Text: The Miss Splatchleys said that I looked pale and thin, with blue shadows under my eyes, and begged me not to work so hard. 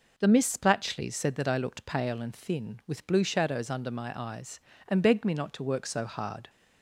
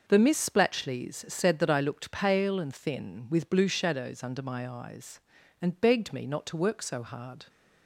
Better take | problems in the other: neither | none

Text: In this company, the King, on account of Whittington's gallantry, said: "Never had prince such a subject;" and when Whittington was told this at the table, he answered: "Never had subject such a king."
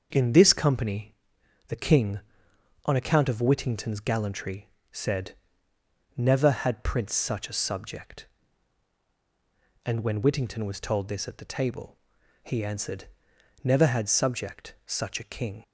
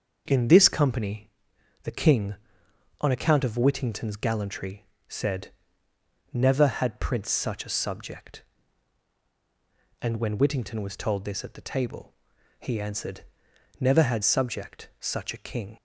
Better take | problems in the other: neither | starts louder than the rest; the same in both

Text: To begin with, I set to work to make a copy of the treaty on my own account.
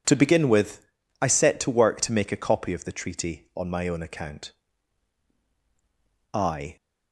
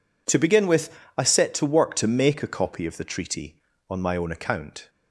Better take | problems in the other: second | goes on to say "I"; slight; from 6.3 s on; 0.44 s long

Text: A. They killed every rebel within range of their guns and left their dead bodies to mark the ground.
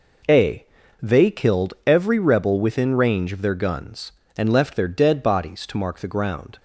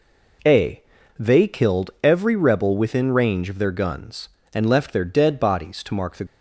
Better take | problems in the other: first | stops before "ground"; at 6.2 s

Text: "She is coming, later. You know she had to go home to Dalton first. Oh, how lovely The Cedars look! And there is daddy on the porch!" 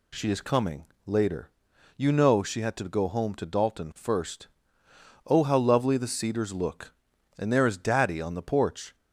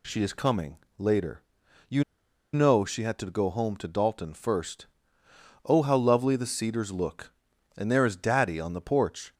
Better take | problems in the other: first | pauses between "You" and "know"; noticeable; at 2.0 s; 0.50 s long

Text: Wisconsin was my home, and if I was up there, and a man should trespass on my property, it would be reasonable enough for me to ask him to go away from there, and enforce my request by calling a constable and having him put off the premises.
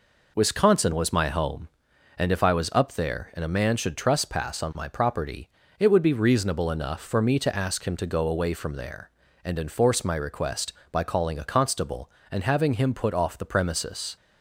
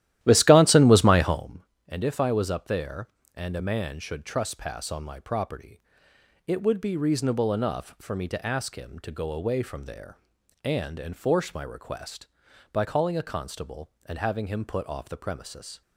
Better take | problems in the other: first | starts louder than the rest; strong; until 1.4 s; 14 dB

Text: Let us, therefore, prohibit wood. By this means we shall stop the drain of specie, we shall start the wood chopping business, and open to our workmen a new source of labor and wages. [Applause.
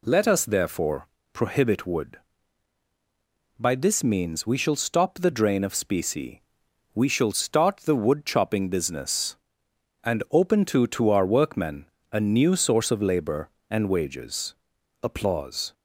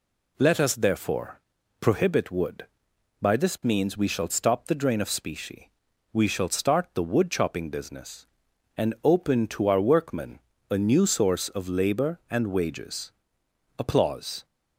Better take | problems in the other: second | says "to" twice; at 10.8 s // pauses between "workmen" and "a"; slight; at 11.8 s; 0.26 s long; slight in the second

